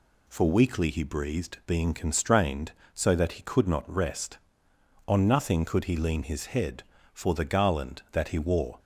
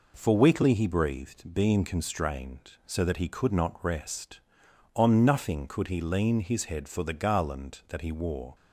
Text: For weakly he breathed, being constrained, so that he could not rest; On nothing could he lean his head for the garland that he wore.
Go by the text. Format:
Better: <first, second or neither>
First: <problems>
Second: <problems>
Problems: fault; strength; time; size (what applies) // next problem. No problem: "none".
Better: neither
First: none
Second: none